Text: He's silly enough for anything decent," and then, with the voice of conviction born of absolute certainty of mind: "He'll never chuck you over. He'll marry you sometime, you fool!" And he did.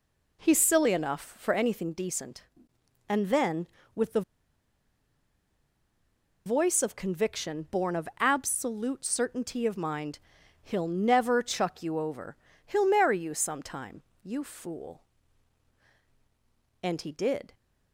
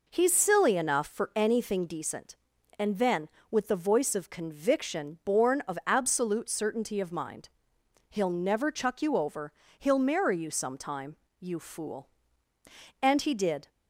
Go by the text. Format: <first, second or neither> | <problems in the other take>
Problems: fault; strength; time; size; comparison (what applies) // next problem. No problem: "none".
second | pauses between "the" and "voice"; strong; at 4.2 s; 2.2 s long